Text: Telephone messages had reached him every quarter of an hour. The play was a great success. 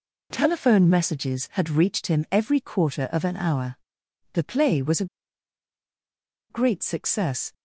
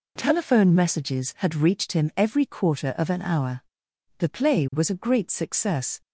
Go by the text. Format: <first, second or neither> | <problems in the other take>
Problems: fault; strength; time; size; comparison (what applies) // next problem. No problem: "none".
second | pauses between "a" and "great"; strong; at 5.0 s; 1.4 s long